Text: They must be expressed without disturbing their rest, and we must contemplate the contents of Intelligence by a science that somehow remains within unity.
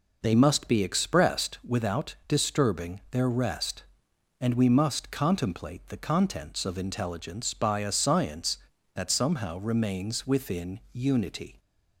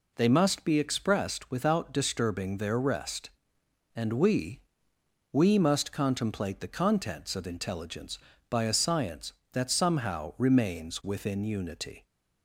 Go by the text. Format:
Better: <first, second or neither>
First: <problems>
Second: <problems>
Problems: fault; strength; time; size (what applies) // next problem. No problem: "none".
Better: first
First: none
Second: says "we" twice; at 5.3 s